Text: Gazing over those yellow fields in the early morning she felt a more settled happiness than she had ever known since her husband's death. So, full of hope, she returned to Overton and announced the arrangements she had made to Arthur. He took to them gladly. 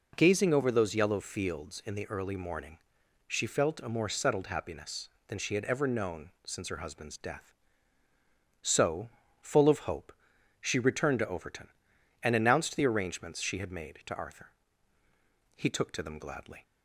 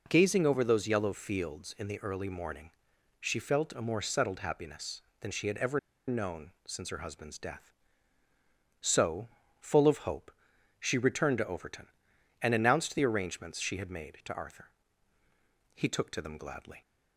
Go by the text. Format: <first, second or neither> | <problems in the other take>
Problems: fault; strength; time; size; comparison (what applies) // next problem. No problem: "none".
first | pauses between "morning" and "she"; noticeable; at 2.6 s; 0.50 s long; noticeable in the first // pauses between "ever" and "known"; slight; at 5.7 s; 0.29 s long // pauses between "known" and "since"; slight; at 6.4 s; 0.16 s long; slight in the first